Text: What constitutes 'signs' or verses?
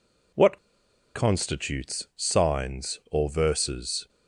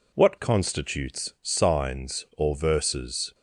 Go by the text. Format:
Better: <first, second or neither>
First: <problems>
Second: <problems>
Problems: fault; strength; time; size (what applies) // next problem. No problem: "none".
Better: second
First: pauses between "What" and "constitutes"; noticeable; at 0.5 s; 0.57 s long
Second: none